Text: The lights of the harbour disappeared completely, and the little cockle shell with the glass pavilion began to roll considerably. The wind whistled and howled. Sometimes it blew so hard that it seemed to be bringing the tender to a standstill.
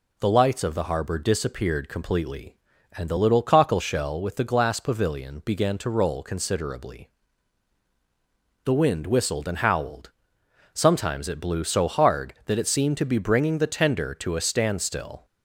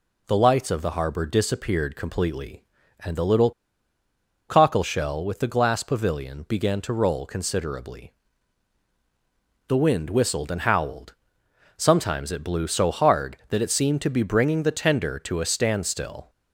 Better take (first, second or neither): first